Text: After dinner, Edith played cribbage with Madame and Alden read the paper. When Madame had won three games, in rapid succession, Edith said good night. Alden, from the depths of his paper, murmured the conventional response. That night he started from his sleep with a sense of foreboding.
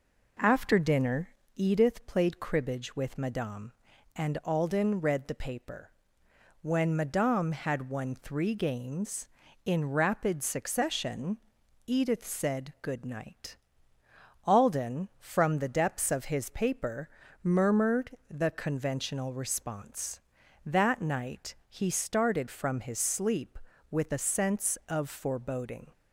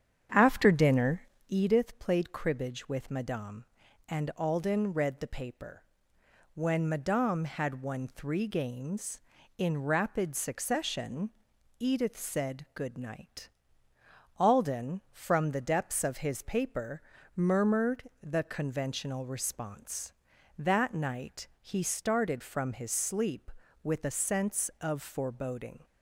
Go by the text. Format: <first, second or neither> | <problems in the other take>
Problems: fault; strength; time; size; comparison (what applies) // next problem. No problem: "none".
first | starts louder than the rest; strong; until 1.7 s; 8.5 dB // pauses between "murmured" and "the"; slight; at 18.0 s; 0.18 s long; slight in the first